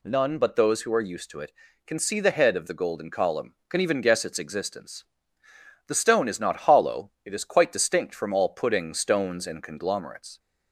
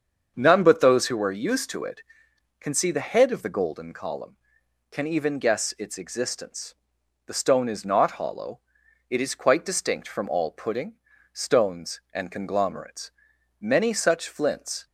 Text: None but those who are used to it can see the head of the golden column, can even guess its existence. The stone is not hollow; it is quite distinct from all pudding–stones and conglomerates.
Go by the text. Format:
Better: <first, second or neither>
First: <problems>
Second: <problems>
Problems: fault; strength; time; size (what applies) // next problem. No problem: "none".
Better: first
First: none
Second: starts louder than the rest; until 1.3 s; 7 dB // goes on to say "Many such flints"; noticeable; from 13.5 s on; 1.2 s long